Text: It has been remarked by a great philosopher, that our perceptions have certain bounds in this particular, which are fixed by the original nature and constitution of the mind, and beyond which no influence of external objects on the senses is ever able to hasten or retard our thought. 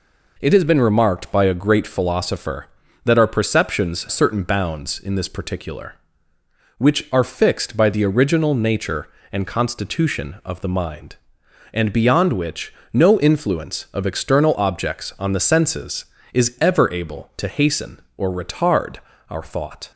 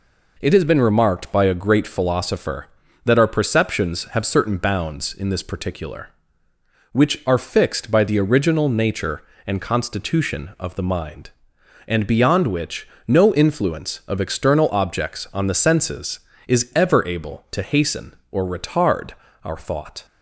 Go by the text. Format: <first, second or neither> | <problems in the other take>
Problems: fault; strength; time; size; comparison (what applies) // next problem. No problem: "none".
second | skips "have"; at 4.0 s // pauses between "which" and "no"; slight; at 12.7 s; 0.22 s long; slight in the second // pauses between "retard" and "our"; slight; at 18.9 s; 0.32 s long; slight in the second